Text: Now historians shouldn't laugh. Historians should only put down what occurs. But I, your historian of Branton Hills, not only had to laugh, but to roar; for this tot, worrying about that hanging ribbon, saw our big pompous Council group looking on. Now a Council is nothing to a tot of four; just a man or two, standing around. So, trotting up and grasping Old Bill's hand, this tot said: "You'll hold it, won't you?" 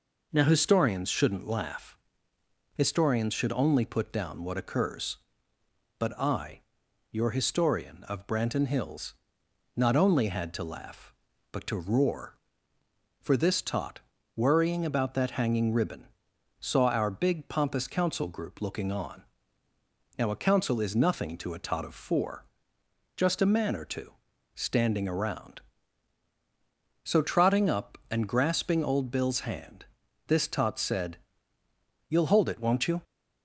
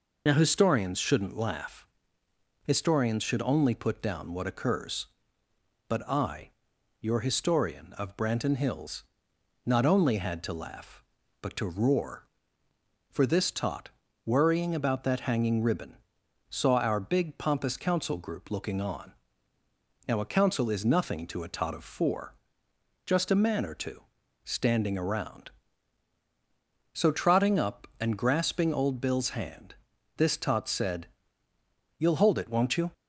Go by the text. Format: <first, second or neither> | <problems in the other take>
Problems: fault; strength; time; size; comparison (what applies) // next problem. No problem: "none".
first | loses the start of "Now"; at 0.2 s; 50 ms